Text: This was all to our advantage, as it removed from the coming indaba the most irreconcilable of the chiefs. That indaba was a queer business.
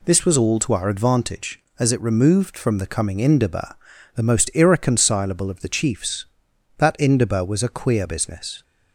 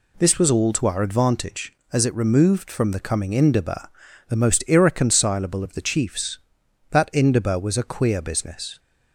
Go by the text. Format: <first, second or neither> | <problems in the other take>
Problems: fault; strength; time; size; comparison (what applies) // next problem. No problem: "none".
neither | pauses between "indaba" and "the"; the same in both